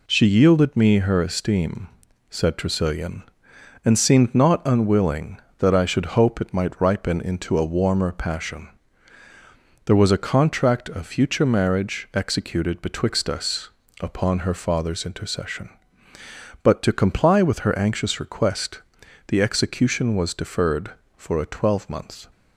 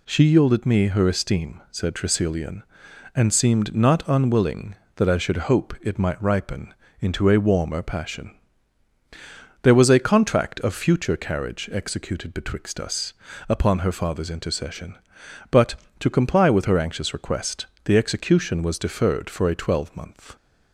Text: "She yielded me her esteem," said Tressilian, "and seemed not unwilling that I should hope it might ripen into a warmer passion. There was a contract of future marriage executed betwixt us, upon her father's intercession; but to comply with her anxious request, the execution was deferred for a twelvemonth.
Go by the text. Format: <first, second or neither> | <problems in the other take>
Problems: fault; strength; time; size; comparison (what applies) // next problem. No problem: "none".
first | pauses between "ripen" and "into"; slight; at 6.7 s; 0.26 s long // says "carriage" for "marriage"; at 11.1 s